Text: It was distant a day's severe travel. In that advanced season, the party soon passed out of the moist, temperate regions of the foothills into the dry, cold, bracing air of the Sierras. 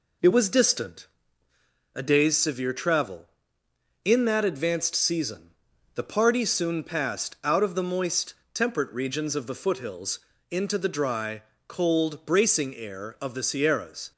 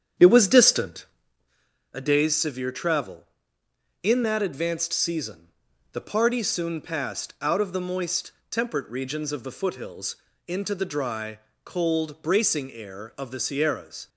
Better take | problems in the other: first | starts louder than the rest; strong; until 1.3 s; 8.5 dB // pauses between "distant" and "a"; noticeable; at 1.0 s; 0.90 s long; noticeable in the first // pauses between "foothills" and "into"; slight; at 10.1 s; 0.30 s long; slight in the first

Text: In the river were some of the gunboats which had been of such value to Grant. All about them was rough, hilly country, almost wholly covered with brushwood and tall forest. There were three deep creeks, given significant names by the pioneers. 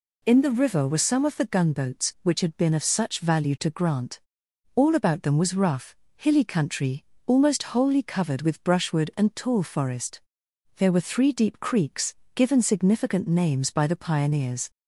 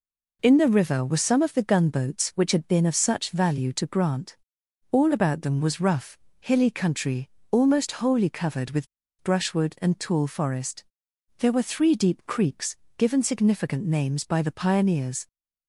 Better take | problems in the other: first | pauses between "with" and "brushwood"; at 8.8 s; 0.38 s long

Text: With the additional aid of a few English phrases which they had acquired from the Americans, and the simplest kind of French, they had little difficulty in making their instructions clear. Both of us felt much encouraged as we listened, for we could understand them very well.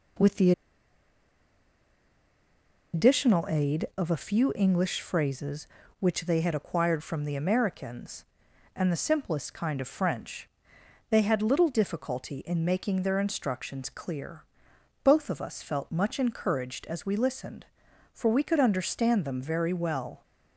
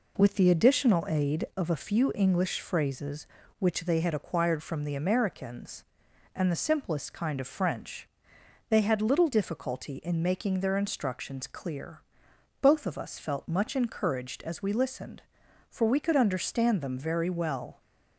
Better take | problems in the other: second | pauses between "the" and "additional"; strong; at 0.5 s; 2.4 s long

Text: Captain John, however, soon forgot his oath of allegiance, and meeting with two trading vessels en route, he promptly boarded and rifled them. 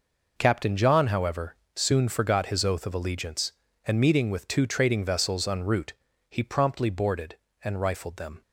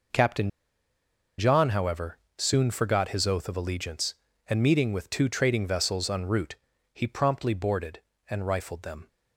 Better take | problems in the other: first | pauses between "Captain" and "John"; noticeable; at 0.4 s; 0.89 s long

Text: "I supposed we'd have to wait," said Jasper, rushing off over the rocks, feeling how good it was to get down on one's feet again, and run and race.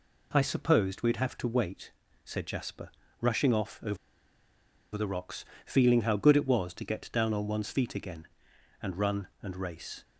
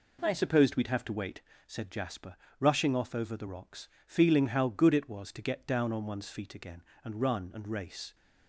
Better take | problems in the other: second | pauses between "over" and "the"; at 3.9 s; 0.98 s long

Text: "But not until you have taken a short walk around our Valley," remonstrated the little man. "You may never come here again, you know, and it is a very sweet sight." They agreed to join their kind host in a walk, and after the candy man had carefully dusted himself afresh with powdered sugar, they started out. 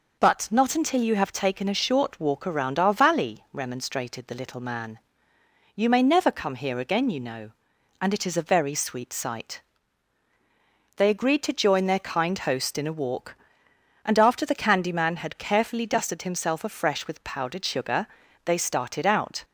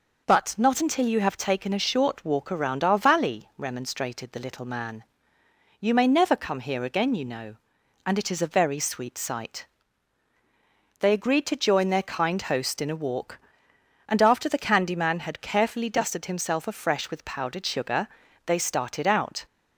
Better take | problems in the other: neither | none

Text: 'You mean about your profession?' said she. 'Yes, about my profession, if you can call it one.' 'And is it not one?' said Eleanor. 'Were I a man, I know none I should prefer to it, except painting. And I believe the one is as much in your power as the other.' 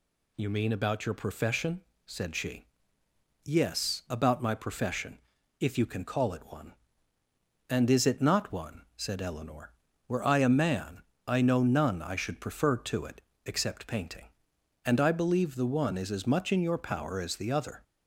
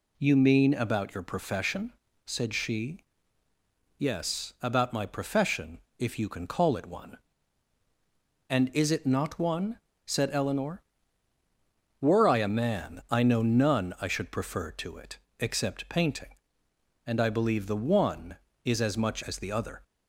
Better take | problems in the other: first | skips "in your power"; at 19.2 s

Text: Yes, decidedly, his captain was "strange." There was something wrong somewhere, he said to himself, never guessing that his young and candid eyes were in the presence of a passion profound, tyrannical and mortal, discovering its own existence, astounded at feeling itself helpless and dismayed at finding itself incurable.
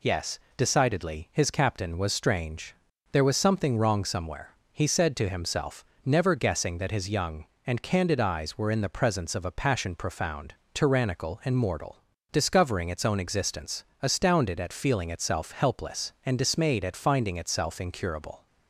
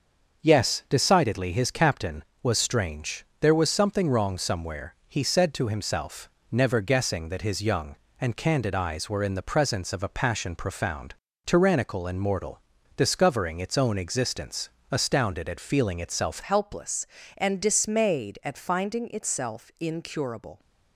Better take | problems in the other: first | starts louder than the rest; until 1.4 s; 6 dB // changes voice at "helpless"; from 16.4 s on; 4.1 s long

